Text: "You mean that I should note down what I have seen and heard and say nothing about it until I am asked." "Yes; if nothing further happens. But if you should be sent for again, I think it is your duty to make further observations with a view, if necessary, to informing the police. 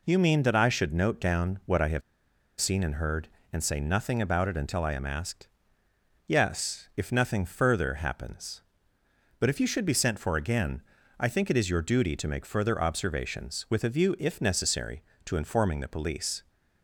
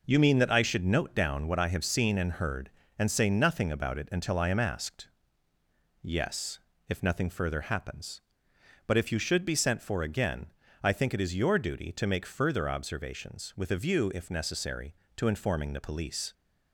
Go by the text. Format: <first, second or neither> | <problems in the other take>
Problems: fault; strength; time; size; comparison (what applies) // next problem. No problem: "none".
second | pauses between "have" and "seen"; noticeable; at 2.0 s; 0.58 s long